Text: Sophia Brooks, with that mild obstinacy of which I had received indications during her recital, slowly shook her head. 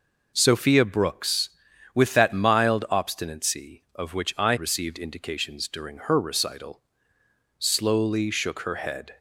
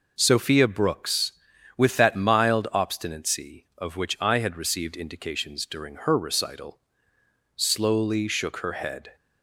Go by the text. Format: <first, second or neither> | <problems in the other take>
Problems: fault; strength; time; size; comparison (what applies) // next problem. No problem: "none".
second | skips "had"; at 4.5 s